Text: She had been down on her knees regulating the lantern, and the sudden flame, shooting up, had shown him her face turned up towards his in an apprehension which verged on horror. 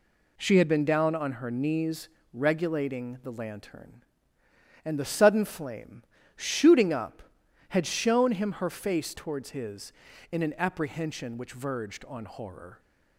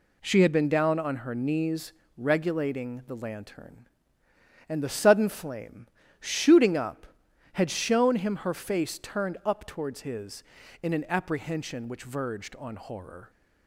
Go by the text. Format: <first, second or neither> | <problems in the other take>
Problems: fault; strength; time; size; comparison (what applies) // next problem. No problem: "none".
second | pauses between "knees" and "regulating"; slight; at 2.0 s; 0.24 s long; slight in the second // skips "turned up"; at 9.1 s